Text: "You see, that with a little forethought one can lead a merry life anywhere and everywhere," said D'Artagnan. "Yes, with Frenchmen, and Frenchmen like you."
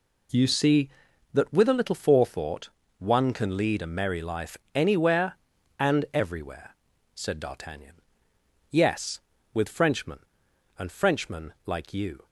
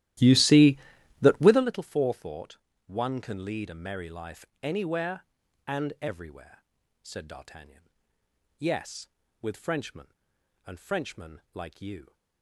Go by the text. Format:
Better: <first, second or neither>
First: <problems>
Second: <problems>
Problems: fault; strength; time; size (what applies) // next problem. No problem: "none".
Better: first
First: pauses between "forethought" and "one"; slight; at 2.7 s; 0.28 s long // pauses between "life" and "anywhere"; slight; at 4.5 s; 0.20 s long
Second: starts louder than the rest; strong; until 1.8 s; 14 dB // pauses between "forethought" and "one"; slight; at 2.5 s; 0.28 s long // pauses between "life" and "anywhere"; slight; at 4.4 s; 0.20 s long